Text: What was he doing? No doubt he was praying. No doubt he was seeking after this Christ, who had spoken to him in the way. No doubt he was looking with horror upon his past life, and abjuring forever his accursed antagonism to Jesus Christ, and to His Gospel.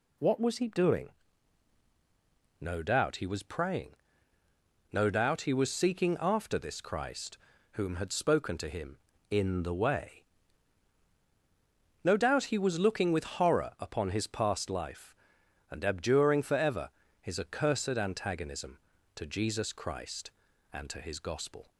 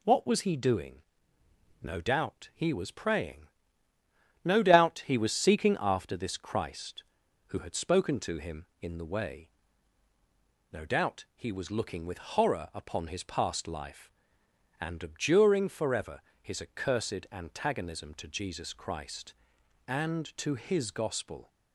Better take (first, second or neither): second